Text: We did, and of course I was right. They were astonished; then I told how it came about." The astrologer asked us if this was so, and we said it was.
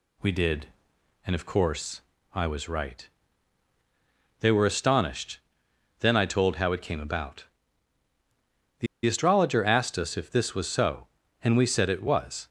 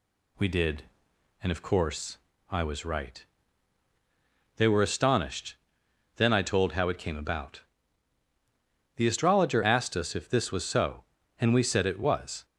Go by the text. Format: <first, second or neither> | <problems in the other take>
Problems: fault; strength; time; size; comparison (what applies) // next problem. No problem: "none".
second | pauses between "course" and "I"; slight; at 2.0 s; 0.32 s long; slight in the second // pauses between "The" and "astrologer"; slight; at 8.8 s; 0.19 s long